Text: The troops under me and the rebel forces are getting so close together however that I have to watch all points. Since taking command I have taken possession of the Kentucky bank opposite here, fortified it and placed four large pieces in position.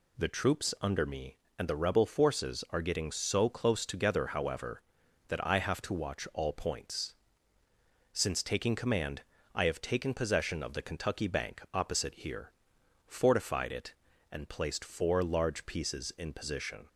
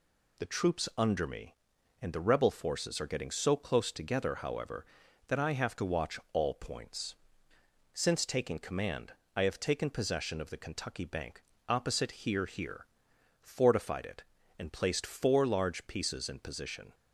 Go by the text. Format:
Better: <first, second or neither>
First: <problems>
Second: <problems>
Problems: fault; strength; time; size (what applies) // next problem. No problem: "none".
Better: first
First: pauses between "command" and "I"; slight; at 9.2 s; 0.32 s long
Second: pauses between "command" and "I"; slight; at 9.1 s; 0.22 s long // pauses between "bank" and "opposite"; slight; at 11.4 s; 0.24 s long // says "here" twice; at 12.4 s